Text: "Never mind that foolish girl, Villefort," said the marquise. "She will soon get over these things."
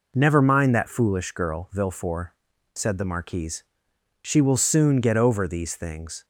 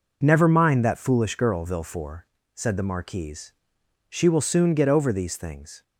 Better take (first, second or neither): neither